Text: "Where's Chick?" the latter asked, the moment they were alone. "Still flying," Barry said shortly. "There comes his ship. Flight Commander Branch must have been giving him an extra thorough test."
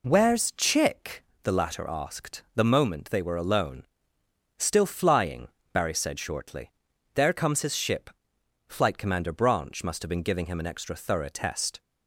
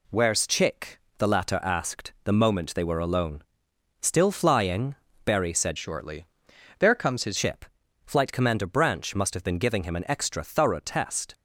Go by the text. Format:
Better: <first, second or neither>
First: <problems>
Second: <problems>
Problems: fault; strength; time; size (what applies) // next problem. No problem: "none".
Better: first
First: none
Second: changes voice from "shortly" to "his"; from 5.7 to 7.3 s; 1.6 s long